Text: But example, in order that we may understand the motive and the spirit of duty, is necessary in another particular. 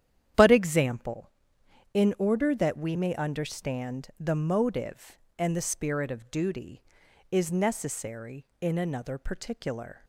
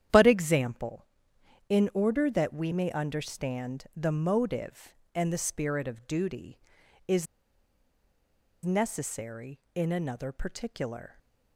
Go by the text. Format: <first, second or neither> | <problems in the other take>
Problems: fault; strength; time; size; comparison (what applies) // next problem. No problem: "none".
first | starts louder than the rest; strong; until 1.7 s; 10 dB; strong in the first // pauses between "is" and "necessary"; strong; at 7.2 s; 1.4 s long